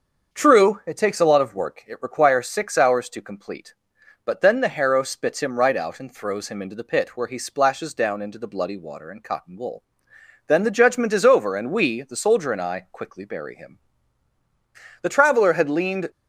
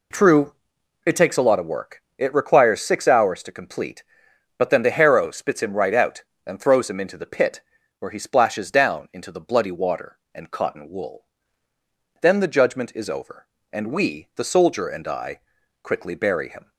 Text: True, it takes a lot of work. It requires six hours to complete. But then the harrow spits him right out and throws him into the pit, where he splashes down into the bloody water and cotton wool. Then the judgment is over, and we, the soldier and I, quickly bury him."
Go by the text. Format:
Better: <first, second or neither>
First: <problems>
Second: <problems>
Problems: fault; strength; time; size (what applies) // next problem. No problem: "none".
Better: second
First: starts louder than the rest; until 1.4 s; 7 dB // goes on to say "The Traveler had leaned"; noticeable; from 15.0 s on; 1.0 s long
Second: none